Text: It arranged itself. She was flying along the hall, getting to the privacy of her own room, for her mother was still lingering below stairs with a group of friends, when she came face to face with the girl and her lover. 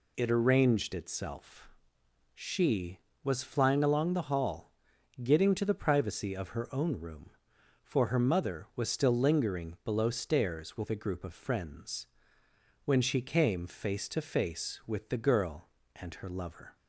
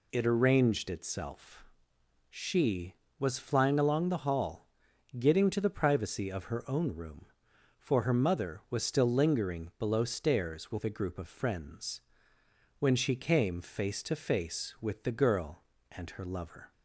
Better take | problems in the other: neither | none

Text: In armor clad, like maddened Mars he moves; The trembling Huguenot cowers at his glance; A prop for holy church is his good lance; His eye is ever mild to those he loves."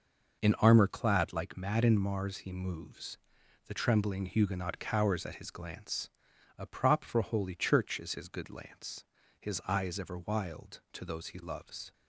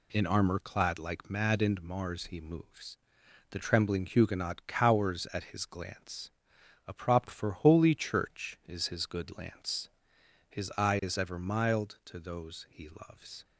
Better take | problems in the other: second | says "wild" for "mild"; at 10.1 s

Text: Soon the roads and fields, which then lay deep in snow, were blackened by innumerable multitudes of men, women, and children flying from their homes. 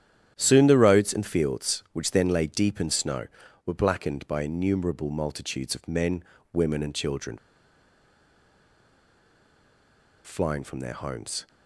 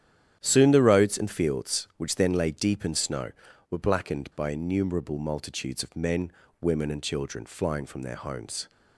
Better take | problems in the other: second | starts louder than the rest; strong; until 1.3 s; 10 dB; strong in the second // pauses between "children" and "flying"; strong; at 7.3 s; 2.8 s long

